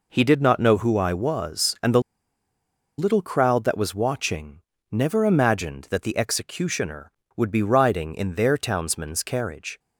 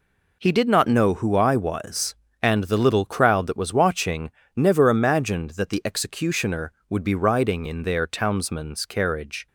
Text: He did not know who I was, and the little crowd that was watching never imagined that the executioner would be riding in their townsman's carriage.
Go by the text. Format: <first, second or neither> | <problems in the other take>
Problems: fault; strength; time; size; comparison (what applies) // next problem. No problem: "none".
second | pauses between "the" and "little"; noticeable; at 2.0 s; 0.97 s long // pauses between "watching" and "never"; slight; at 4.5 s; 0.32 s long; slight in the second